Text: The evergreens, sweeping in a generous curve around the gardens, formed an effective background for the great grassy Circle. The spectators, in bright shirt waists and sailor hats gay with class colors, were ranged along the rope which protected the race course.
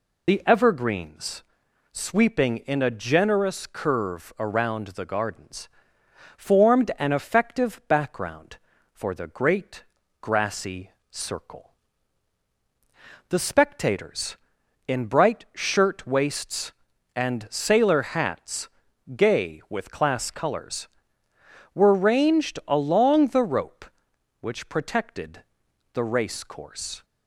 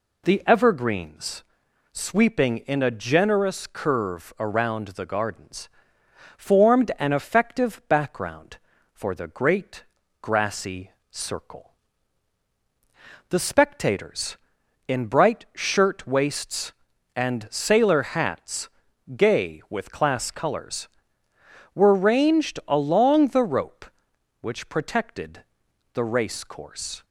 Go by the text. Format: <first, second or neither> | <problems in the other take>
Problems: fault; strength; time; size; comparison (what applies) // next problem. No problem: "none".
second | loses the start of "The"; at 0.2 s; 35 ms // pauses between "great" and "grassy"; slight; at 9.8 s; 0.36 s long; slight in the second // pauses between "grassy" and "Circle"; slight; at 10.9 s; 0.26 s long; slight in the second // pauses between "hats" and "gay"; noticeable; at 18.6 s; 0.48 s long; noticeable in the second // pauses between "protected" and "the"; noticeable; at 25.4 s; 0.48 s long; noticeable in the second